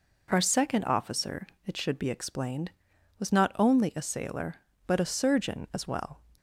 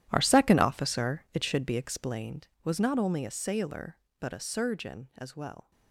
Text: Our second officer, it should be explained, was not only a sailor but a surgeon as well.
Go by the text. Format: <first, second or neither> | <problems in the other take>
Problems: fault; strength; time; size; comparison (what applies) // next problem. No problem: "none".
first | gets quieter; strong; throughout; 16.5 dB